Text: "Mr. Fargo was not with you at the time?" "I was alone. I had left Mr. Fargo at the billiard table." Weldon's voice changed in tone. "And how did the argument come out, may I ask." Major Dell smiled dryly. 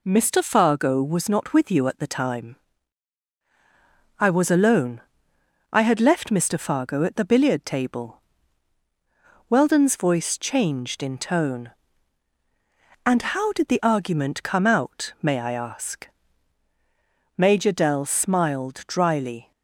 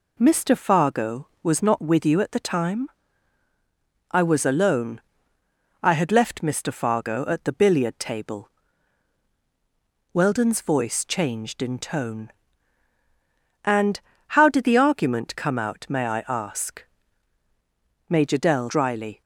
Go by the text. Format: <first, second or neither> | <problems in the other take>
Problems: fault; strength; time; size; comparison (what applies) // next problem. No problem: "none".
first | pauses between "And" and "how"; slight; at 13.9 s; 0.34 s long // skips "smiled"; at 18.6 s